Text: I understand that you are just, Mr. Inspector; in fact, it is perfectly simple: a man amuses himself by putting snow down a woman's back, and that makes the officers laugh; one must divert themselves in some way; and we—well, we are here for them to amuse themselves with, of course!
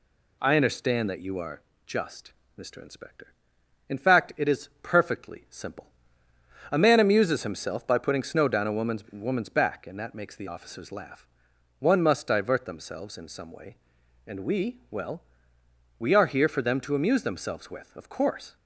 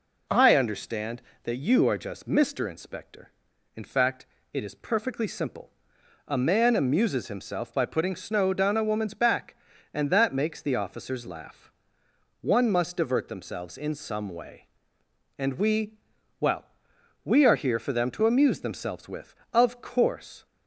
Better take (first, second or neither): second